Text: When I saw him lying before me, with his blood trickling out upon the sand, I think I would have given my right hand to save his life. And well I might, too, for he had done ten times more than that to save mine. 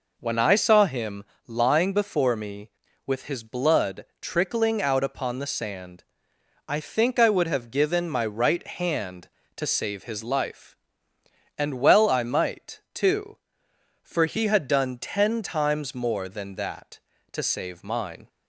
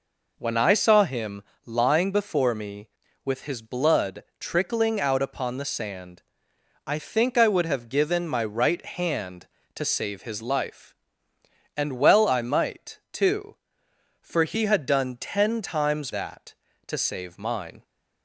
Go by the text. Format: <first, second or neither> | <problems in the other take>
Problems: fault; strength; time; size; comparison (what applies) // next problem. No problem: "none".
first | pauses between "him" and "lying"; slight; at 1.4 s; 0.22 s long; slight in the first // pauses between "blood" and "trickling"; slight; at 4.2 s; 0.16 s long; slight in the first // skips "more than"; at 16.1 s